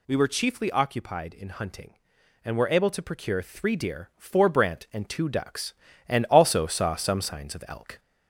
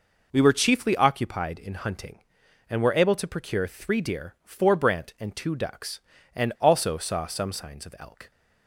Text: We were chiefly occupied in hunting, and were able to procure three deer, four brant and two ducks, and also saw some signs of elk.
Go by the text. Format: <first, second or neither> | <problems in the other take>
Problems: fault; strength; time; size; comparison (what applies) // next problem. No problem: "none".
second | gets louder; slight; throughout; 2 dB